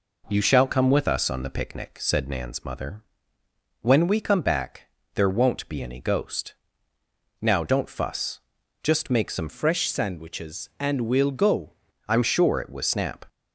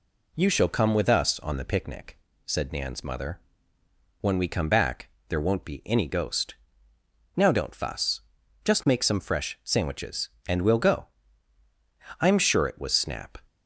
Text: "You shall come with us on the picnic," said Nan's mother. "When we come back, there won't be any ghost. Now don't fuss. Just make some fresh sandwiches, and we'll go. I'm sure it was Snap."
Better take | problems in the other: second | changes voice from "fresh" to "go"; from 9.4 to 11.7 s; 2.3 s long

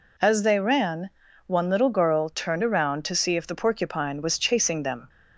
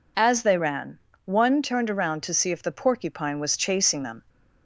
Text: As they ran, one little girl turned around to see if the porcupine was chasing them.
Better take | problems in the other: first | skips "little girl"; at 1.6 s

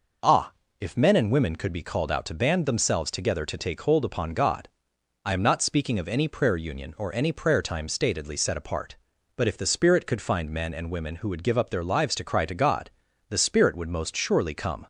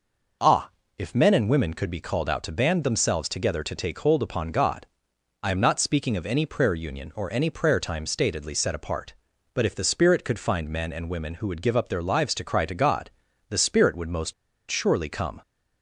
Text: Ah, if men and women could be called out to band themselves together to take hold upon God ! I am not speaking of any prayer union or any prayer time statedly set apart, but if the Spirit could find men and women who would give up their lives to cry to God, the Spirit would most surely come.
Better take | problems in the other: first | pauses between "most" and "surely"; at 14.3 s; 0.37 s long

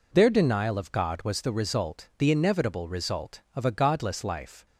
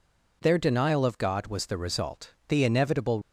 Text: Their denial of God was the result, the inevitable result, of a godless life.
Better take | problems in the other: first | stops before "result of a godless life"; at 3.2 s

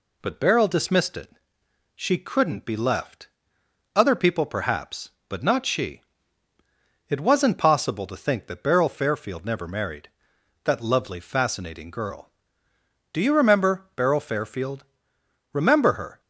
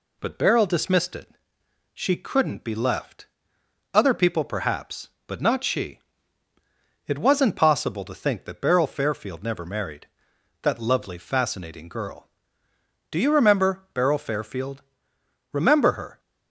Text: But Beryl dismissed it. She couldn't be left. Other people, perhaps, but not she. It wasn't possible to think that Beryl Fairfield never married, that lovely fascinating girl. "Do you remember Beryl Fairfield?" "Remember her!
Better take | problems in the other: neither | none

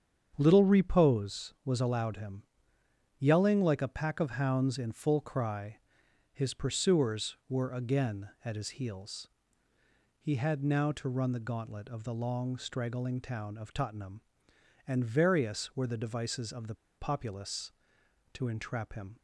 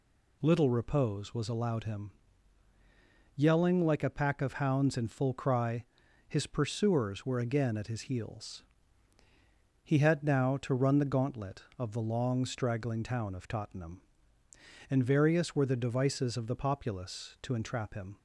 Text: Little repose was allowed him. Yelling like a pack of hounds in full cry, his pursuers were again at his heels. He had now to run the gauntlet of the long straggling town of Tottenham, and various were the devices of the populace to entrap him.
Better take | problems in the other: second | starts louder than the rest; strong; until 1.3 s; 7.5 dB // pauses between "the" and "populace"; slight; at 16.7 s; 0.23 s long

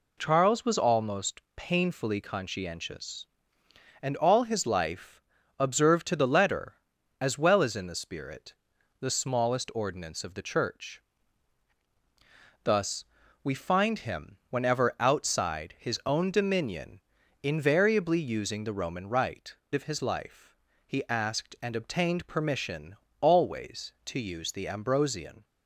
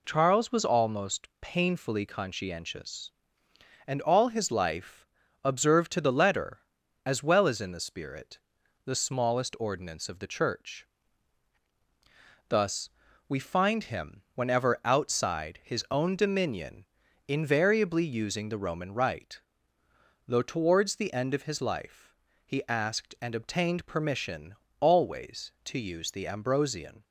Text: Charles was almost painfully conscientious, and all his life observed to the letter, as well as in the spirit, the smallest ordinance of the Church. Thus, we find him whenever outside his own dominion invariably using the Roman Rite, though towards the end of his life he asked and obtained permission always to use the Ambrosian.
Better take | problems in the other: second | pauses between "life" and "observed"; at 5.2 s; 0.38 s long; also in the second // pauses between "dominion" and "invariably"; at 16.9 s; 0.42 s long; also in the second // skips "though towards the end"; at 19.6 s // pauses between "life" and "he"; slight; at 20.5 s; 0.32 s long; slight in the second // pauses between "permission" and "always"; slight; at 22.9 s; 0.26 s long; slight in the second

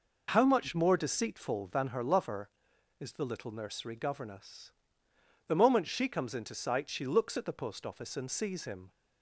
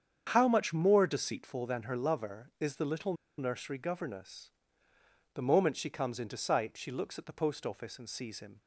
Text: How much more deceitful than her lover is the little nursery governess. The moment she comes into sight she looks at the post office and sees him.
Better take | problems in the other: first | starts louder than the rest; strong; until 1.3 s; 7.5 dB // pauses between "little" and "nursery"; slight; at 3.1 s; 0.24 s long

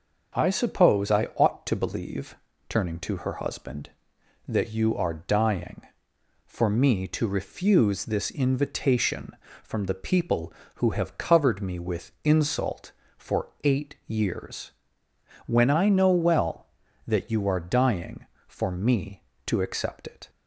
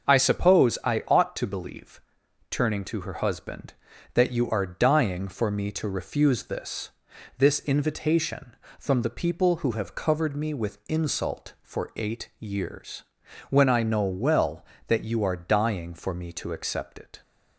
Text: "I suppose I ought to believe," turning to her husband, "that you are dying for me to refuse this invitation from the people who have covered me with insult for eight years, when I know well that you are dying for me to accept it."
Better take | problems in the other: first | starts louder than the rest; until 1.1 s; 7 dB; also in the first // says "this" twice; at 7.3 s

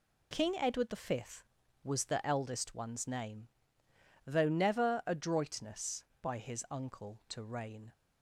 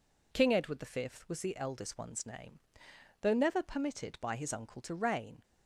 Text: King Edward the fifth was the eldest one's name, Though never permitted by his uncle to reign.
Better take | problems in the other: second | says "adroitness" for "permitted"; at 5.0 s

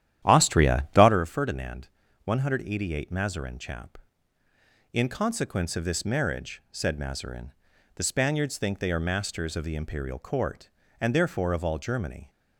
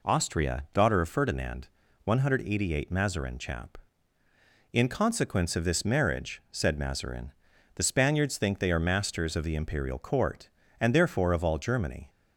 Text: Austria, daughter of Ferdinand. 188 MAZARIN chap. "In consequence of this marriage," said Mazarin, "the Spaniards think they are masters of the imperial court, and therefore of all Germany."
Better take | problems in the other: second | starts louder than the rest; strong; until 1.2 s; 11.5 dB

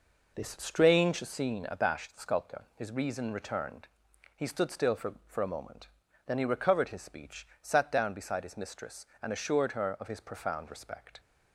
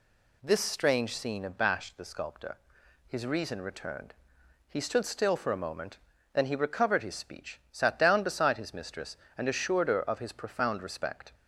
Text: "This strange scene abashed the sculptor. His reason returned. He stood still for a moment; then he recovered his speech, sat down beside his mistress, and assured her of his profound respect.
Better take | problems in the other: second | says "for" twice; at 5.2 s

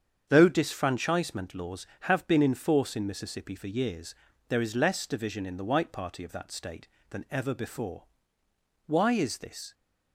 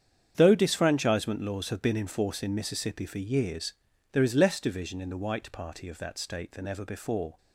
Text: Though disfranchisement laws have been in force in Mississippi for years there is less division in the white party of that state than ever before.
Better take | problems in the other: second | starts louder than the rest; strong; until 1.3 s; 7.5 dB; strong in the second // pauses between "years" and "there"; slight; at 4.1 s; 0.36 s long; also in the second // goes on to say "Why is this"; noticeable; from 8.8 s on; 0.88 s long

